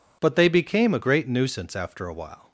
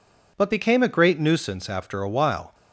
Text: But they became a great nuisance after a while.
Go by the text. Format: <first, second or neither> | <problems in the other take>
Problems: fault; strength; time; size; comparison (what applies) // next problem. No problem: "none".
first | skips "they"; at 0.5 s